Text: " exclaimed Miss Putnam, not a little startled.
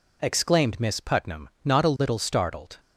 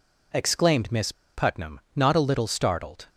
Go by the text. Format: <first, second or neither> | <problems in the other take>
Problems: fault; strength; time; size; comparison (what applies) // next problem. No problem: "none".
first | pauses between "Miss" and "Putnam"; slight; at 1.1 s; 0.22 s long